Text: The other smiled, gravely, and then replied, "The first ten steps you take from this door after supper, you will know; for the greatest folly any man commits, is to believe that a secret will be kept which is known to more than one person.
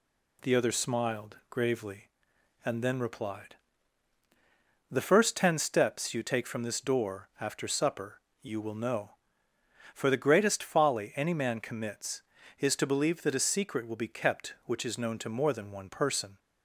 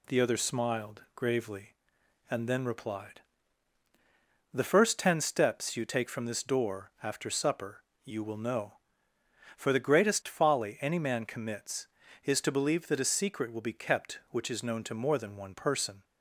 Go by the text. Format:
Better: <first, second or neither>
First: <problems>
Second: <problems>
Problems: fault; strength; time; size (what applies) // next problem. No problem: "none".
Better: neither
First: none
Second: none